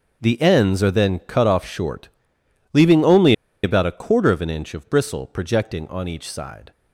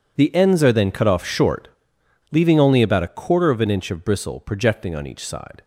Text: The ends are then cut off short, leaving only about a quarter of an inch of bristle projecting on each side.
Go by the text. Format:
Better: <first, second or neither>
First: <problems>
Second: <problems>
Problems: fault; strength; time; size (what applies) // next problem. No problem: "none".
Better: second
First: pauses between "only" and "about"; slight; at 3.3 s; 0.31 s long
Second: none